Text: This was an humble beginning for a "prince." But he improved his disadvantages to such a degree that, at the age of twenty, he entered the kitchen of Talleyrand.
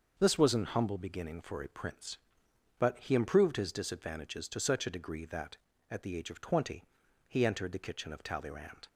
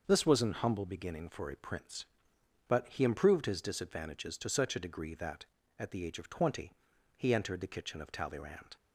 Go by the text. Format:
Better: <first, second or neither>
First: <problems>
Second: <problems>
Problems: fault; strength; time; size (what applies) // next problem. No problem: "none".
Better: neither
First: starts louder than the rest; until 1.1 s; 6 dB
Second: starts louder than the rest; until 1.0 s; 6 dB